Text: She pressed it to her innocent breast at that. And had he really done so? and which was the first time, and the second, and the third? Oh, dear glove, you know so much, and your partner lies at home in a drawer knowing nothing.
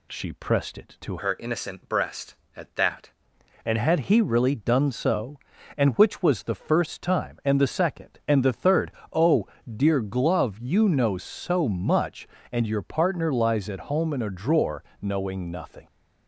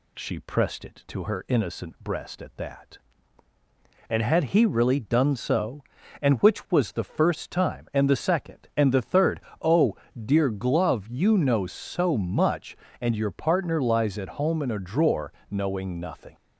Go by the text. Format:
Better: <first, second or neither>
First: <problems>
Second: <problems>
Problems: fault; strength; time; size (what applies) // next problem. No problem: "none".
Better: second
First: changes voice from "her" to "that"; from 1.1 to 3.0 s; 1.9 s long // pauses between "drawer" and "knowing"; slight; at 14.8 s; 0.18 s long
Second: pauses between "drawer" and "knowing"; slight; at 15.3 s; 0.18 s long